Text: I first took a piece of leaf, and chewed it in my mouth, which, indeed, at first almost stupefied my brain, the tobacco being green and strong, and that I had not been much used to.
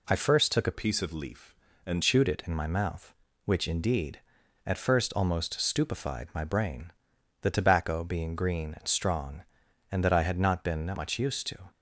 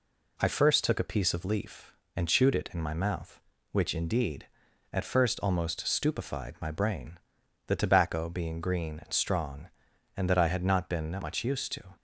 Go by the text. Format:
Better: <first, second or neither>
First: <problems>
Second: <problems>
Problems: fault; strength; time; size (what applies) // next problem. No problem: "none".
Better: second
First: changes voice from "piece" to "and"; from 0.7 to 2.0 s; 1.3 s long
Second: none